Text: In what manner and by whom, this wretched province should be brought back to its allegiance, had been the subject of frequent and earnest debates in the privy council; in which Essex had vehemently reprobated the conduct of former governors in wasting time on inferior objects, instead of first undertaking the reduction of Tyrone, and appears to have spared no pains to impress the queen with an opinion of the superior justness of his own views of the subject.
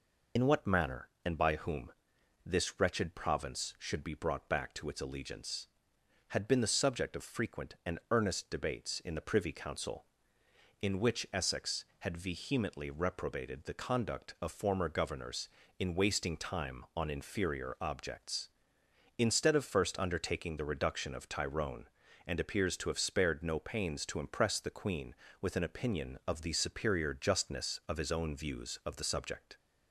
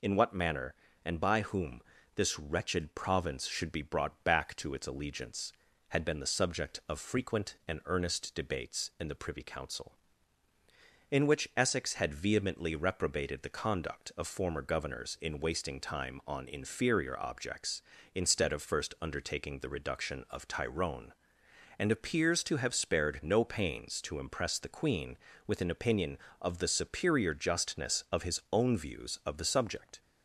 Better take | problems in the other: second | loses the start of "In"; at 0.3 s; 50 ms

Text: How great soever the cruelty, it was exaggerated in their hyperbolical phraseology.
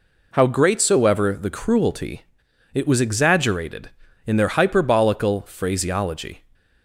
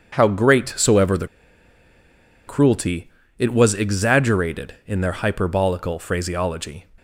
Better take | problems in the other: first | starts louder than the rest; strong; until 1.1 s; 7.5 dB // pauses between "the" and "cruelty"; at 1.2 s; 1.2 s long

